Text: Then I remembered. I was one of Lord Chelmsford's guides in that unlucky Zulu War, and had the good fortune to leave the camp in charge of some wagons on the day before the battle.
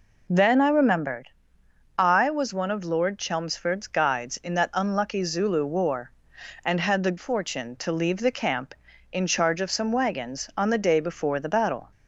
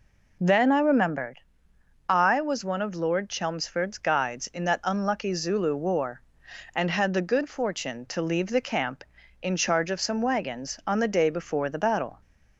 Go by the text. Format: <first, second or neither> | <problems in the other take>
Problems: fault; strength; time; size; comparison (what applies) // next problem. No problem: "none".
second | skips "good"; at 7.1 s